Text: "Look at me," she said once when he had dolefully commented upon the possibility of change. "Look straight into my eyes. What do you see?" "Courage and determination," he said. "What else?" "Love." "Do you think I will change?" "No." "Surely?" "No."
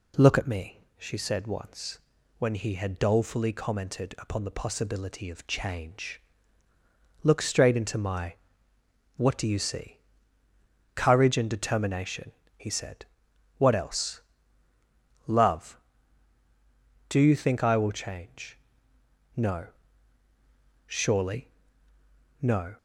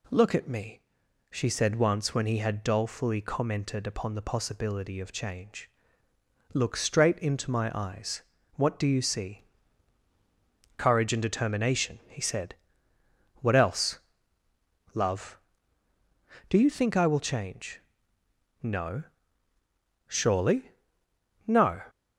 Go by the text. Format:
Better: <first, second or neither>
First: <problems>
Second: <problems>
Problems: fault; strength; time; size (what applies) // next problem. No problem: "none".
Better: second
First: pauses between "once" and "when"; at 1.9 s; 0.40 s long // skips "eyes"; at 8.7 s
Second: none